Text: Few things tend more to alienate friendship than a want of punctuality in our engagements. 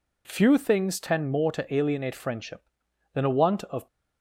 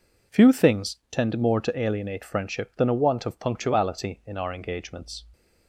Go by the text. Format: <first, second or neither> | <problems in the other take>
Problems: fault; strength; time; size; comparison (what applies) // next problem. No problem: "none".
second | stops before "punctuality in our engagements"; at 3.8 s